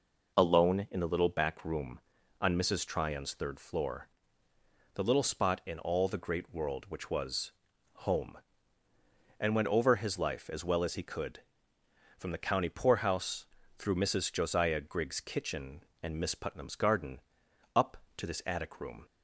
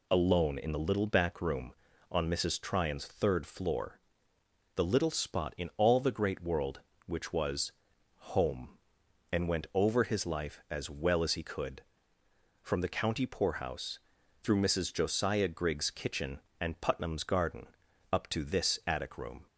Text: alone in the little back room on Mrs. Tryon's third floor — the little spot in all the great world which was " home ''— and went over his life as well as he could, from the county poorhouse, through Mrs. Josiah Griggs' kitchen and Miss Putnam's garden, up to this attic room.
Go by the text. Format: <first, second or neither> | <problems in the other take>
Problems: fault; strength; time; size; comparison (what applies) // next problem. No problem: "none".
first | skips "Miss"; at 16.8 s